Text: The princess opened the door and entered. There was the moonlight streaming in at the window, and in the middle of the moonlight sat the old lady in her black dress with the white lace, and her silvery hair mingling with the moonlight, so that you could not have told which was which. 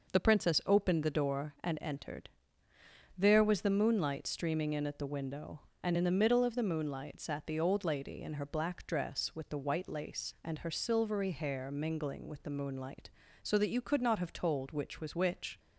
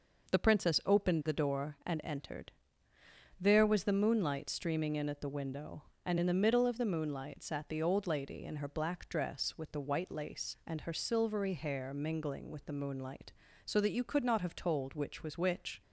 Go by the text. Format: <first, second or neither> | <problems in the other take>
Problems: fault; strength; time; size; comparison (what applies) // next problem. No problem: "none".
neither | none